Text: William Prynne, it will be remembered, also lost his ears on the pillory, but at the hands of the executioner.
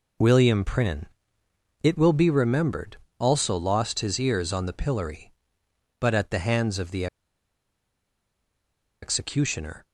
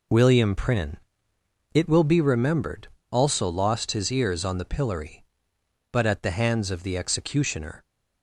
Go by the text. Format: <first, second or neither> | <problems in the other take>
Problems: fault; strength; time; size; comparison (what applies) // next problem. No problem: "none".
second | pauses between "the" and "executioner"; strong; at 7.0 s; 1.9 s long